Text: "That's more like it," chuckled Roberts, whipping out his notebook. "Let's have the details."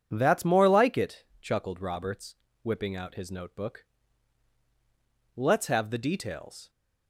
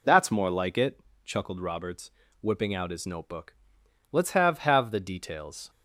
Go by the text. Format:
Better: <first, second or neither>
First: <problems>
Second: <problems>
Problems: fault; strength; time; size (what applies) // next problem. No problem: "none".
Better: first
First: none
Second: says "have" twice; at 4.5 s